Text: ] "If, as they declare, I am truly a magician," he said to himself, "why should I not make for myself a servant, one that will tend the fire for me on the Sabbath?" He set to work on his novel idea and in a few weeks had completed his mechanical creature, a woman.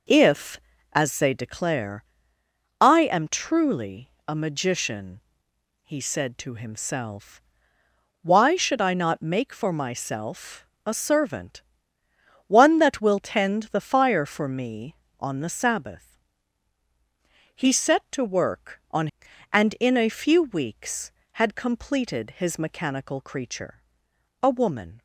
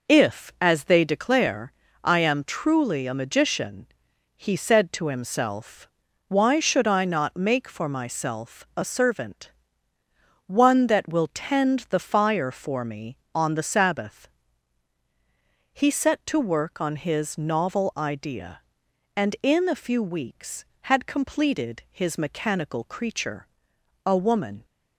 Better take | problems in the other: second | pauses between "truly" and "a"; slight; at 4.0 s; 0.16 s long // pauses between "myself" and "a"; slight; at 10.6 s; 0.20 s long // skips "his novel idea"; at 19.3 s

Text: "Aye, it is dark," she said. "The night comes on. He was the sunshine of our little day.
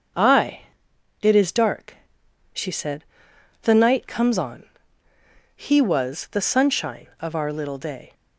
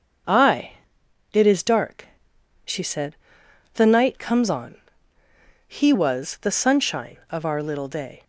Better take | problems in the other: neither | starts louder than the rest; the same in both

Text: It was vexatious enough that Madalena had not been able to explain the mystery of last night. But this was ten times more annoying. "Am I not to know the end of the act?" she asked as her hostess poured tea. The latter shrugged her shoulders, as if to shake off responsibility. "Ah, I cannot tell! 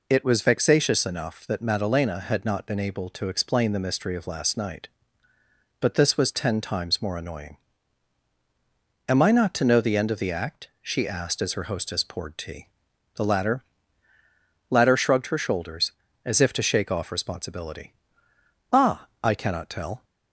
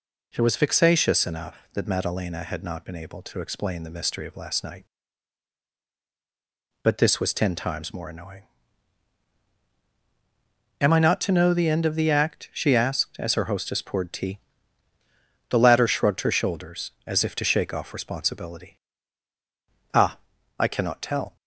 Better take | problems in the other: second | says "latter" twice; at 14.6 s

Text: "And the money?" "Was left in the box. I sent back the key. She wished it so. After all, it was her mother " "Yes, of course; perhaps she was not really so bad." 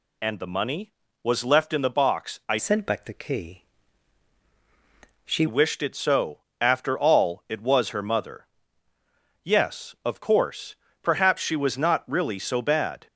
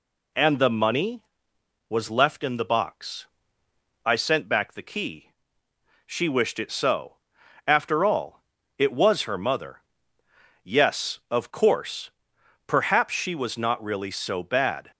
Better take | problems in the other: second | changes voice from "sent" to "She"; from 2.5 to 5.4 s; 2.9 s long

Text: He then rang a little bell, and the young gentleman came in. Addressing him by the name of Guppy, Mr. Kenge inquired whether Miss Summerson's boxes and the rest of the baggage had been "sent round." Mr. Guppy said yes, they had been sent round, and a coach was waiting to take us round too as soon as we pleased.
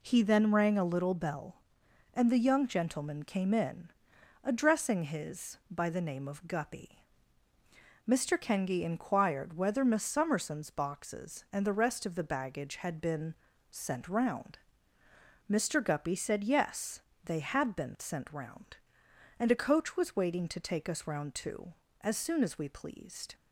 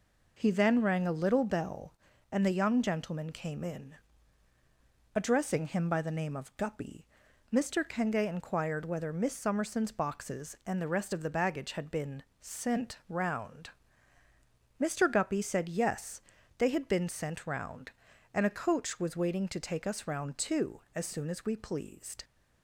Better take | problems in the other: second | says "his" for "him"; at 5.0 s // pauses between "been" and "sent"; slight; at 13.3 s; 0.34 s long; slight in the second

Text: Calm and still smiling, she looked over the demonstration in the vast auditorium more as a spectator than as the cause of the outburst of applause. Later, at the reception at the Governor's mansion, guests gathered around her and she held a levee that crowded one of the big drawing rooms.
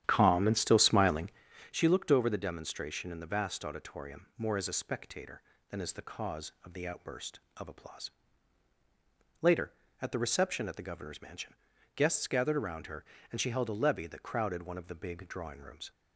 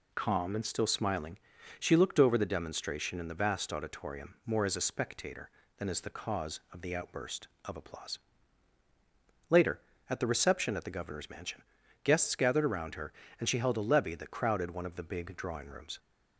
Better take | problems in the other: second | starts louder than the rest; strong; until 1.5 s; 10.5 dB

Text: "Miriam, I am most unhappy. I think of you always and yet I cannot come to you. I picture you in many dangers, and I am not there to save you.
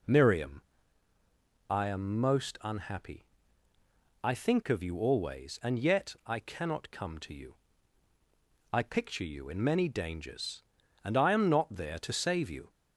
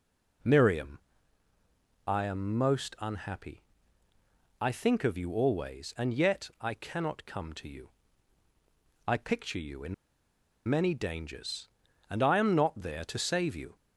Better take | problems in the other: first | pauses between "in" and "many"; noticeable; at 9.9 s; 0.73 s long

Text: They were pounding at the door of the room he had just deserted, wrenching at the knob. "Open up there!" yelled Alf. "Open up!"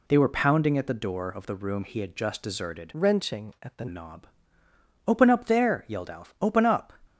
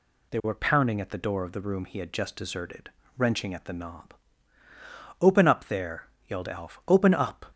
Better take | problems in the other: second | changes voice from "wrenching" to "the"; from 2.9 to 3.8 s; 0.9 s long

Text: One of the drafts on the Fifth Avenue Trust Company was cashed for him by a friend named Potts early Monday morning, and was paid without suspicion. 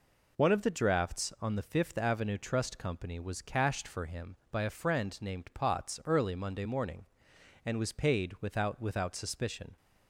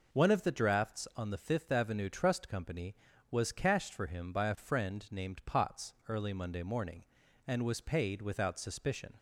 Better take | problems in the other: second | says "without" twice; at 8.8 s

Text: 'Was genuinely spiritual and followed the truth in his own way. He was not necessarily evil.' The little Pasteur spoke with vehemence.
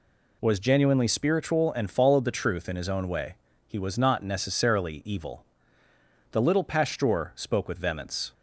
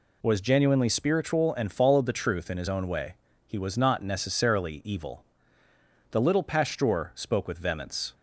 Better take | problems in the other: neither | none

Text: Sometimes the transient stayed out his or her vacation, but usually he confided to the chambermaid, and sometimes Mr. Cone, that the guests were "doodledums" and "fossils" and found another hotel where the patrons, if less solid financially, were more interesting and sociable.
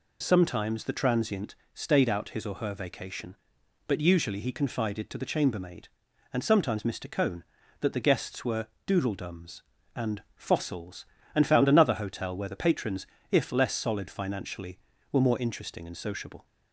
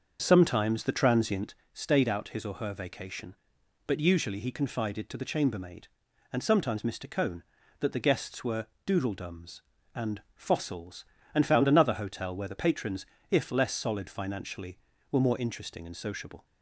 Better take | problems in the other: first | starts louder than the rest; until 1.6 s; 6.5 dB // pauses between "transient" and "stayed"; slight; at 1.5 s; 0.18 s long; slight in the first // pauses between "were" and "doodledums"; slight; at 8.6 s; 0.18 s long; slight in the first

